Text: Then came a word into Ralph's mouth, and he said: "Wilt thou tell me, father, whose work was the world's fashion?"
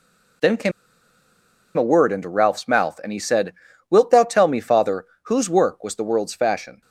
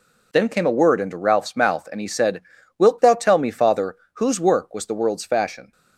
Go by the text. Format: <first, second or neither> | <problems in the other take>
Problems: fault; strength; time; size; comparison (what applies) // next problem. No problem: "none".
second | pauses between "came" and "a"; at 0.7 s; 1.0 s long